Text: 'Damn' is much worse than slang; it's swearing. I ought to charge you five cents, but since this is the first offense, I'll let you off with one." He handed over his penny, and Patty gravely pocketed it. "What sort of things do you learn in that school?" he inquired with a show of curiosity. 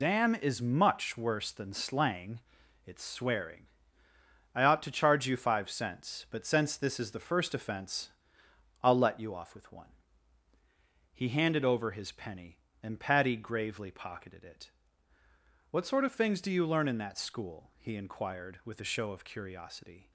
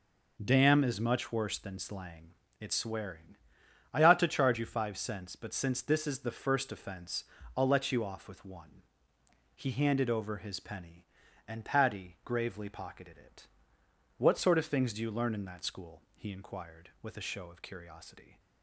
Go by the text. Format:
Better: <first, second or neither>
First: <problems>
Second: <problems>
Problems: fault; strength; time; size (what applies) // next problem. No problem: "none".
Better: second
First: loses the start of "Damn"; at 0.0 s; 45 ms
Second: none